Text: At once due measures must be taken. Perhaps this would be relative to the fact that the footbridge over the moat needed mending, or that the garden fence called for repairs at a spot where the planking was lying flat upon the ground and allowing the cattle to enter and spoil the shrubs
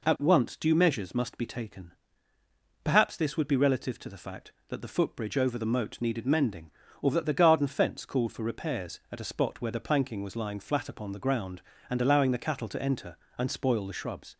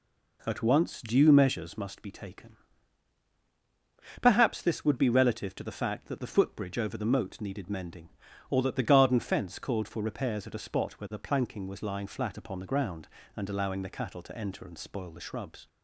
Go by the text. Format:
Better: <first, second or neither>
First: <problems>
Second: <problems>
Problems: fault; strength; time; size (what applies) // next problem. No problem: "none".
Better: neither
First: none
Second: none